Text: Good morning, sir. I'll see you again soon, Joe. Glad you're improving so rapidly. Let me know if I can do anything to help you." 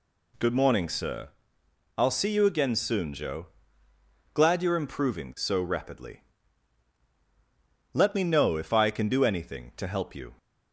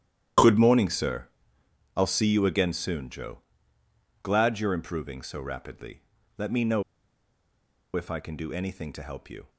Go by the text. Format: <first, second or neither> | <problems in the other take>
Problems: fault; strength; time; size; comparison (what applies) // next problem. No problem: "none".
first | starts louder than the rest; strong; until 2.1 s; 10.5 dB // pauses between "know" and "if"; at 6.8 s; 1.1 s long